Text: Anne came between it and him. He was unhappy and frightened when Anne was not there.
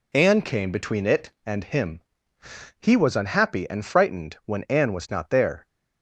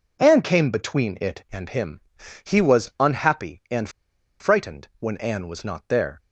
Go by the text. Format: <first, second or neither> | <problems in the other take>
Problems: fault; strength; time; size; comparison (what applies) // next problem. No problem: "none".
first | pauses between "and" and "frightened"; noticeable; at 3.8 s; 0.51 s long